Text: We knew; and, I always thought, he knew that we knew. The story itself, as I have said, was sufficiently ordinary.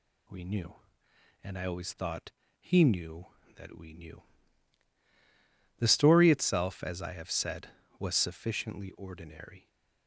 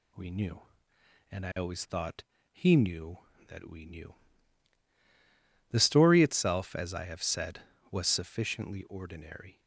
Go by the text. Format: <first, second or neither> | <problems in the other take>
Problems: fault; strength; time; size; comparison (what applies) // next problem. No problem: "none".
neither | none